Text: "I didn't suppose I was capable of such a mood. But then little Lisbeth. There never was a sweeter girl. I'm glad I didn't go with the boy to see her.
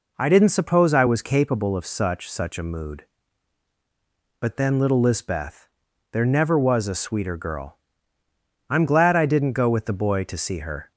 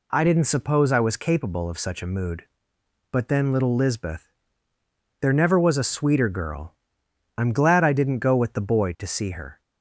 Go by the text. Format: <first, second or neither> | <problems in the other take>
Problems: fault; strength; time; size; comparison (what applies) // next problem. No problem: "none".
second | says "such" twice; at 2.2 s